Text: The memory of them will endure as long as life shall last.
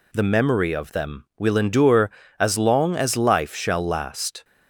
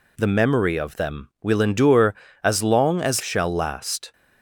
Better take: first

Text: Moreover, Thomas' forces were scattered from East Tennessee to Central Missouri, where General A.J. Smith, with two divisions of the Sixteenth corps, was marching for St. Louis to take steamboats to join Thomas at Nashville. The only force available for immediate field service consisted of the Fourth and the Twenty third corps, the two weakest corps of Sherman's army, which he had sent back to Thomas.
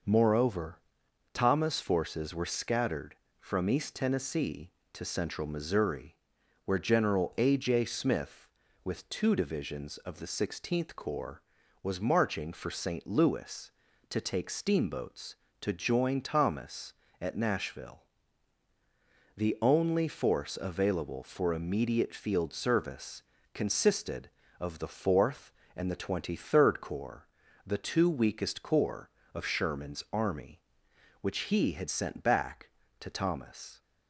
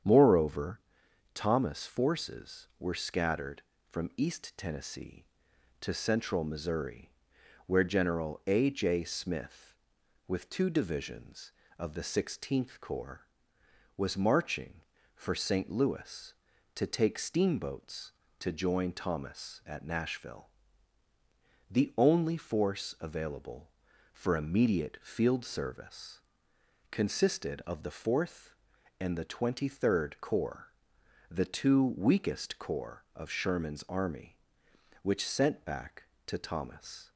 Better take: first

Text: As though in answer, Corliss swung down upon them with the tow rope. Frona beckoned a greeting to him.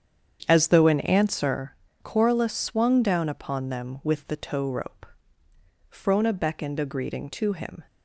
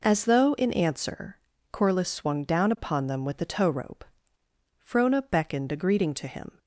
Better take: second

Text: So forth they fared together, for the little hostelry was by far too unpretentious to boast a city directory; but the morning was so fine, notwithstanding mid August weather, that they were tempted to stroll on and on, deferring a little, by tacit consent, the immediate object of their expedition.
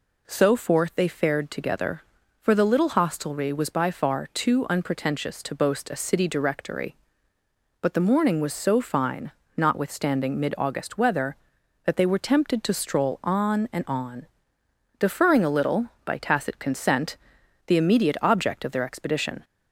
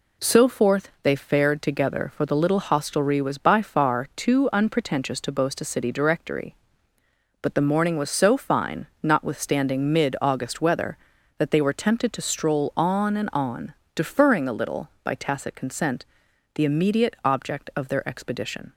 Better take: neither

